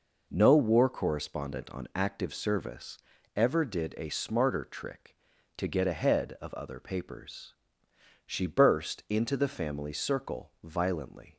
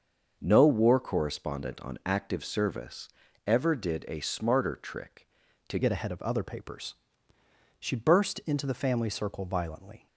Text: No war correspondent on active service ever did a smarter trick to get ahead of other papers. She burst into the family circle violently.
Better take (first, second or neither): first